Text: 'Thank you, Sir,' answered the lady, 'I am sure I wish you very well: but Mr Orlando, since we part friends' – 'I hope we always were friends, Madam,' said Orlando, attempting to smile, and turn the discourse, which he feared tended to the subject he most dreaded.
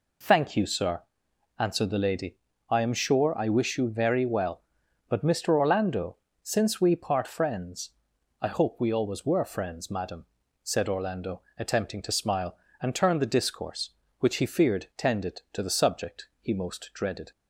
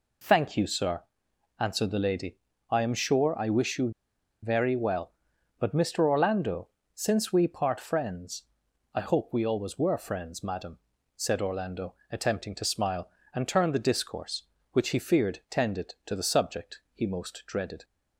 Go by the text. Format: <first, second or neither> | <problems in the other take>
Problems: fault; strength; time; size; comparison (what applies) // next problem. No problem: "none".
first | pauses between "you" and "very"; noticeable; at 3.9 s; 0.52 s long